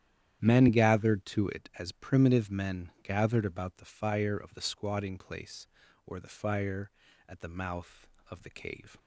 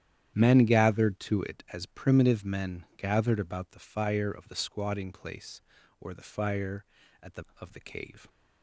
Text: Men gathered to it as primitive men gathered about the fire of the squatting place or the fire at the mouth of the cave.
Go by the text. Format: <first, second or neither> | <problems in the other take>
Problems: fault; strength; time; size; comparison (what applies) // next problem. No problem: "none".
first | starts louder than the rest; strong; until 1.3 s; 10.5 dB; strong in the first // skips "mouth"; at 7.5 s